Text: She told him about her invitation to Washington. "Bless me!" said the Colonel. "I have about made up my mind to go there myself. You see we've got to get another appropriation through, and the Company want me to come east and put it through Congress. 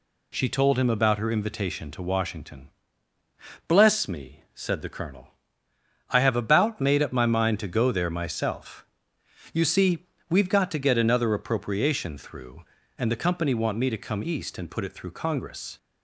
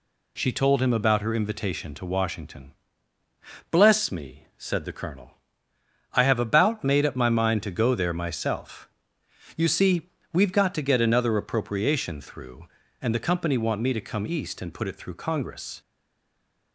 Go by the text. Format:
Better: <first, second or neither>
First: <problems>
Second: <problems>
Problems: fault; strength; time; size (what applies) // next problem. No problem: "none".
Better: first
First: pauses between "see" and "we've"; slight; at 10.0 s; 0.24 s long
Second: pauses between "see" and "we've"; slight; at 10.1 s; 0.24 s long // stays silent after the last word; slight; from 15.8 s on; 0.9 s long